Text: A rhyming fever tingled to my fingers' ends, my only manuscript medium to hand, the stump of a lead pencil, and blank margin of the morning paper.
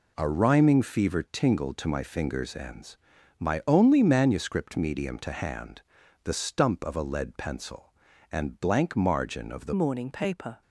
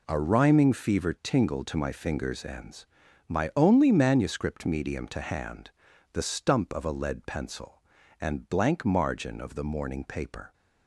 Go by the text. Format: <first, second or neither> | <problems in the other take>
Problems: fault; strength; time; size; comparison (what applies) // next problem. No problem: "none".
second | changes voice at "morning"; from 9.7 s on; 0.9 s long